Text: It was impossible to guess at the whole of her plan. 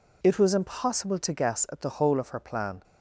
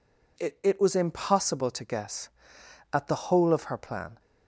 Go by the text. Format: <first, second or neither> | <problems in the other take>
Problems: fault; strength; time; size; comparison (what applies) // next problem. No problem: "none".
first | says "It" twice; at 0.6 s